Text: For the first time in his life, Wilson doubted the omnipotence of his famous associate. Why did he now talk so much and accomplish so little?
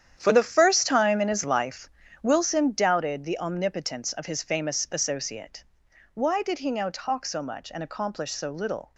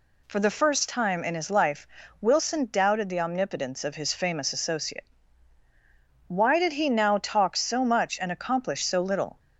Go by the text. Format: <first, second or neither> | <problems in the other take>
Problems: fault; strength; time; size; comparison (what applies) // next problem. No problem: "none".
second | gets quieter; strong; throughout; 12.5 dB